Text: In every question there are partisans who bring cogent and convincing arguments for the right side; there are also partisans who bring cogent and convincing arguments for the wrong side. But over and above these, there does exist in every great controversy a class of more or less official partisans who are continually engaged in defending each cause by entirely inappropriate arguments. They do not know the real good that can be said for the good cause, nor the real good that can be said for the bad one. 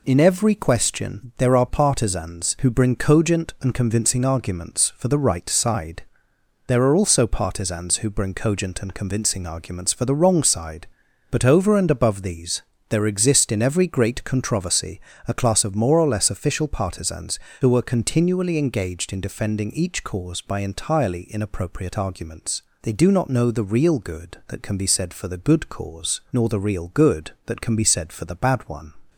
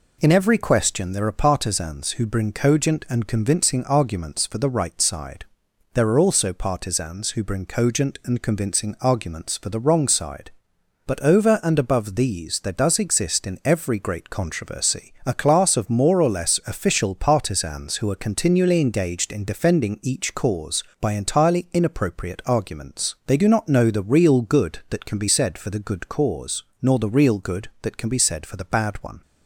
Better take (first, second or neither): second